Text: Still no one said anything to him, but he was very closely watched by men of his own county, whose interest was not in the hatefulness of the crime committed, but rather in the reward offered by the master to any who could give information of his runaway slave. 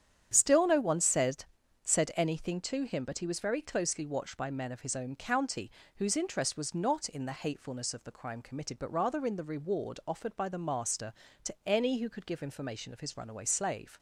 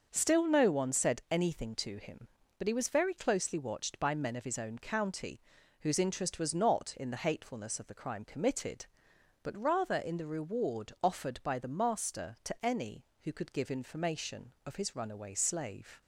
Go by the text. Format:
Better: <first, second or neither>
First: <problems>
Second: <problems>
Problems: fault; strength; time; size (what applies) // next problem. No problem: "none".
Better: second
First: starts louder than the rest; strong; until 1.3 s; 9 dB // says "said" twice; at 1.8 s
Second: starts louder than the rest; until 1.1 s; 6.5 dB